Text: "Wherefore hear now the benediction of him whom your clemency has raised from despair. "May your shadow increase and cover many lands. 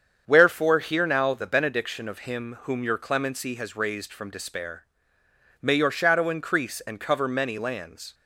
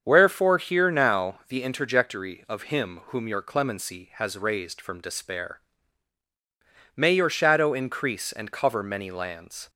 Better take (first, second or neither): first